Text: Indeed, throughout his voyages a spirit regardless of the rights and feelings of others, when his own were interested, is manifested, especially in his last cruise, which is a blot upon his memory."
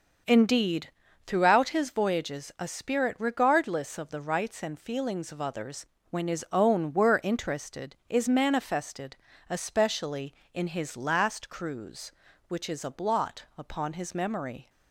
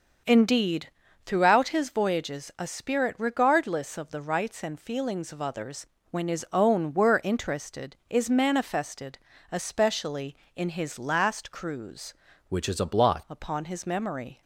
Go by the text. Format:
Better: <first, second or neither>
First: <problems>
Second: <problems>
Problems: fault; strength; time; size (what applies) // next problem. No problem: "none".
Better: first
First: starts louder than the rest; until 1.6 s; 6.5 dB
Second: starts louder than the rest; until 1.6 s; 6.5 dB // changes voice from "which" to "blot"; from 12.4 to 13.2 s; 0.8 s long